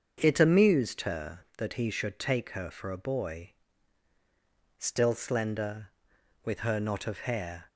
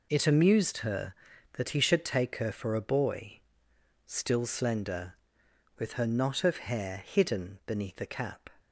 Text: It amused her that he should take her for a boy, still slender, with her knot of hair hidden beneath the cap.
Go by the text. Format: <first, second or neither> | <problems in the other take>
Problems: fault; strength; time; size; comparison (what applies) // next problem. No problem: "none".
second | starts louder than the rest; until 1.2 s; 7 dB // stops before "hidden beneath the cap"; at 7.6 s